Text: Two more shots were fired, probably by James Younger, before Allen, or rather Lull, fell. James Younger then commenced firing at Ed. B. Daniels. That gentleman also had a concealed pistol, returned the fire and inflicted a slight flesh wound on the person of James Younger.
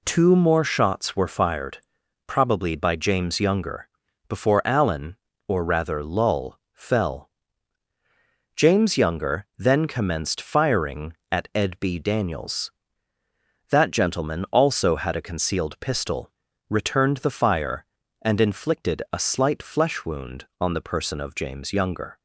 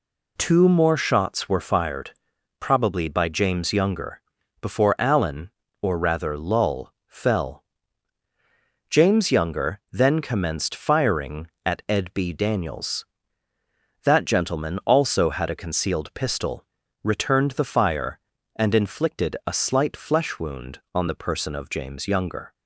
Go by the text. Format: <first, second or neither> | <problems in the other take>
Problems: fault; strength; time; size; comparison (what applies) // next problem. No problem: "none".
neither | none